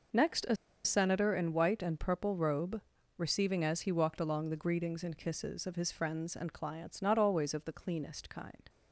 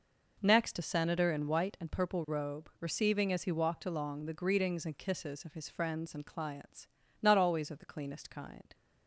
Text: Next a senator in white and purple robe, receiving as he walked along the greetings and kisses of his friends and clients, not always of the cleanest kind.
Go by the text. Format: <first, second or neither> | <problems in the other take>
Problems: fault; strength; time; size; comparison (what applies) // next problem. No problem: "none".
second | pauses between "a" and "senator"; slight; at 0.5 s; 0.28 s long